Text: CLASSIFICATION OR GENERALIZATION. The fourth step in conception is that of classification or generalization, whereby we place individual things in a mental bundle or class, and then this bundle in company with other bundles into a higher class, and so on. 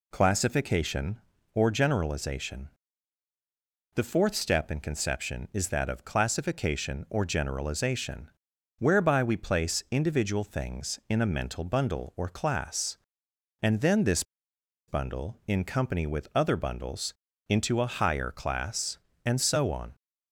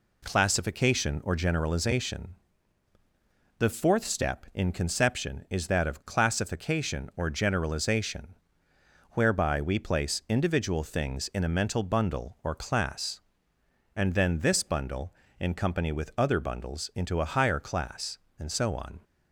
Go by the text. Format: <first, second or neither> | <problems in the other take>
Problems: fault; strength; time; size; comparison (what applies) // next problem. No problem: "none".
second | pauses between "this" and "bundle"; noticeable; at 14.2 s; 0.65 s long // pauses between "bundles" and "into"; slight; at 17.1 s; 0.36 s long